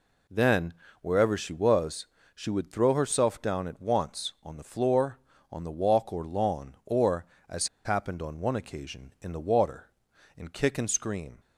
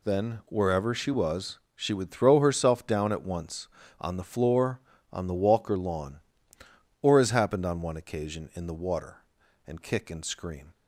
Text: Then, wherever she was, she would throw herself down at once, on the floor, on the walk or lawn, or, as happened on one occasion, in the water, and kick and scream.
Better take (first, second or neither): second